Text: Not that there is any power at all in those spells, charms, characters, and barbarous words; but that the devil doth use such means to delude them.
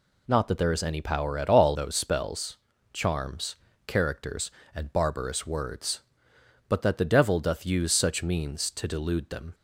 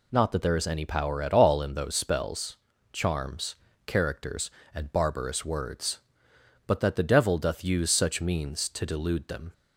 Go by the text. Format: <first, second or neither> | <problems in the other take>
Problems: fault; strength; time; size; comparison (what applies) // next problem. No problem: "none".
second | skips "in"; at 1.7 s